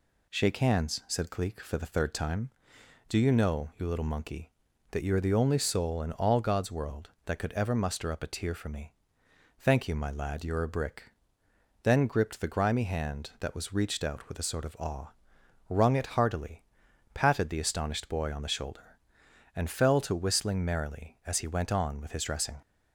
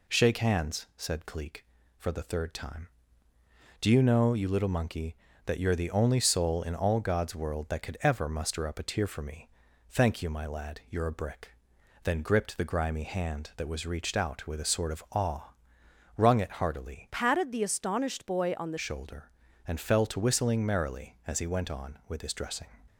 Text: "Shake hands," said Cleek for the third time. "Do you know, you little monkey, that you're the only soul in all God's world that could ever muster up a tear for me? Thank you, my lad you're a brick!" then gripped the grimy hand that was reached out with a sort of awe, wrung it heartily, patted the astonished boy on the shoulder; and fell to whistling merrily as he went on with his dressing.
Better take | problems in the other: first | changes voice from "patted" to "the"; from 17.1 to 18.7 s; 1.6 s long

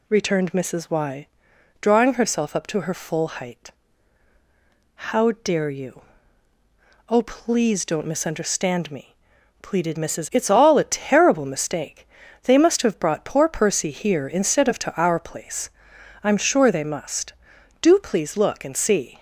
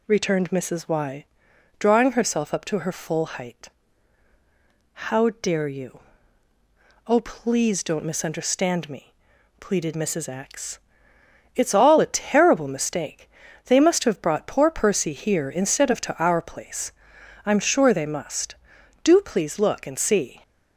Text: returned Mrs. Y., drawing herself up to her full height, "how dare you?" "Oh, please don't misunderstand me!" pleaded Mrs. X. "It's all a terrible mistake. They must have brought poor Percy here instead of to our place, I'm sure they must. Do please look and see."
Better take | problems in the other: second | skips "X"; at 10.3 s

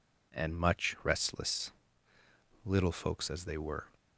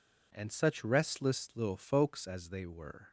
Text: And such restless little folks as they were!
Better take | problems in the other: second | says "much" for "such"; at 0.5 s // pauses between "restless" and "little"; noticeable; at 1.7 s; 0.92 s long

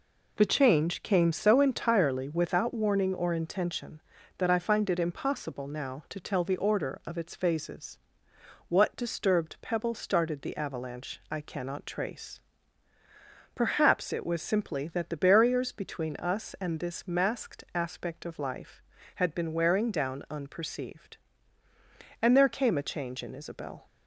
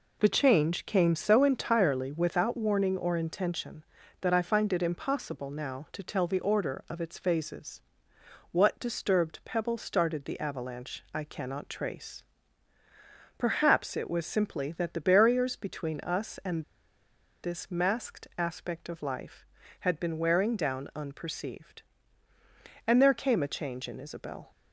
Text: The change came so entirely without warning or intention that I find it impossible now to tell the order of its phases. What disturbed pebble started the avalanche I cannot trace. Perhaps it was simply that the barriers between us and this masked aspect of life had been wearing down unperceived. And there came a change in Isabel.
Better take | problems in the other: first | pauses between "and" and "this"; noticeable; at 16.6 s; 0.80 s long

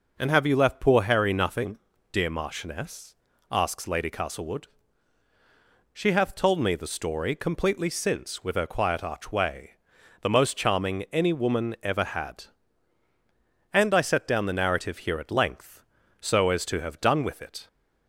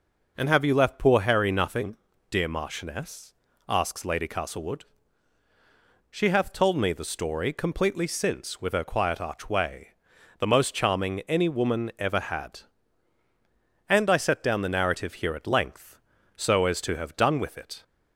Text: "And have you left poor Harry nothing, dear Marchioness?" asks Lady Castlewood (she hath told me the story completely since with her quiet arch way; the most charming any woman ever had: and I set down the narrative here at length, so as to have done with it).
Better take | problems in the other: neither | none

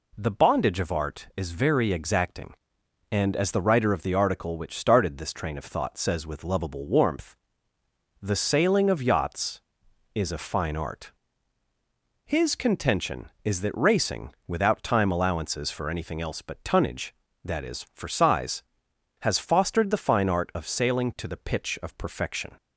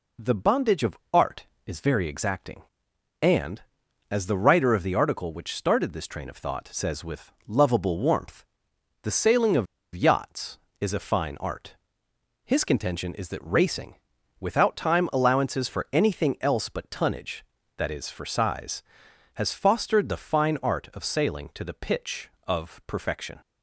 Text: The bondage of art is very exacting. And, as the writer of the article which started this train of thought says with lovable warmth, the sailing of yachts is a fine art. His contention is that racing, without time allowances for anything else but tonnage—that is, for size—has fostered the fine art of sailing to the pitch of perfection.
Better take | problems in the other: first | pauses between "of" and "yachts"; slight; at 9.6 s; 0.28 s long

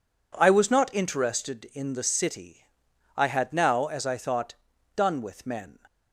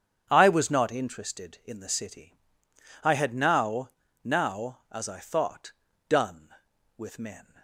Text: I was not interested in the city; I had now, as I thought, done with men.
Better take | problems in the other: first | starts louder than the rest; strong; until 1.3 s; 8.5 dB // says "now" twice; at 4.2 s

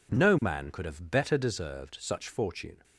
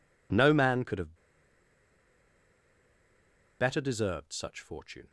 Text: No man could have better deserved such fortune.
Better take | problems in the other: first | pauses between "have" and "better"; strong; at 1.1 s; 2.4 s long

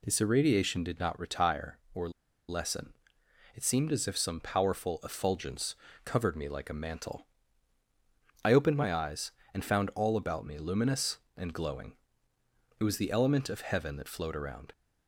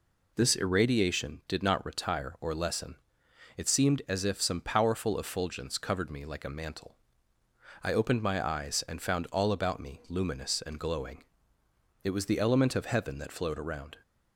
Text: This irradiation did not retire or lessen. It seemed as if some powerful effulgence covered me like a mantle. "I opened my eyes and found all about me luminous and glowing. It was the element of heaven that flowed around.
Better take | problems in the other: second | pauses between "or" and "lessen"; at 2.0 s; 0.39 s long // pauses between "effulgence" and "covered"; slight; at 5.7 s; 0.28 s long

